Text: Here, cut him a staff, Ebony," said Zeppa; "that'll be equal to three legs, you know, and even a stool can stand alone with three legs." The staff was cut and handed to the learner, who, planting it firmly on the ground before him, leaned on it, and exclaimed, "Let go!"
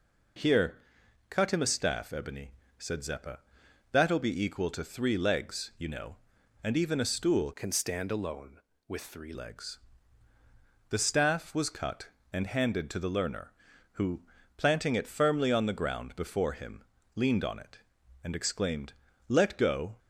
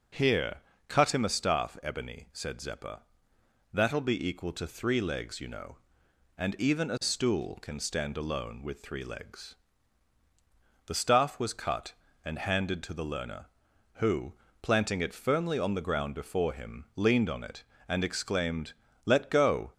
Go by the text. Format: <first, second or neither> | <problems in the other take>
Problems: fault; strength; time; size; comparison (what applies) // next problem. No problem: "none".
second | changes voice from "can" to "three"; from 7.5 to 9.3 s; 1.8 s long